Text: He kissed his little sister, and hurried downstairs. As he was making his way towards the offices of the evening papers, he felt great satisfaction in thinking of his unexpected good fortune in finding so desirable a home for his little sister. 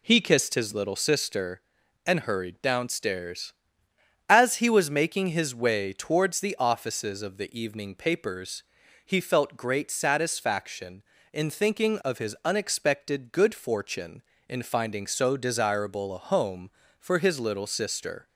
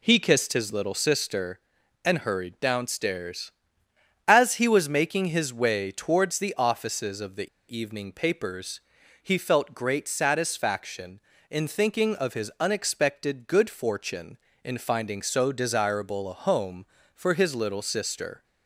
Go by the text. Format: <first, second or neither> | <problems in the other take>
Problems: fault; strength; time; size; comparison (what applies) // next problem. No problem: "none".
first | pauses between "the" and "evening"; slight; at 7.4 s; 0.28 s long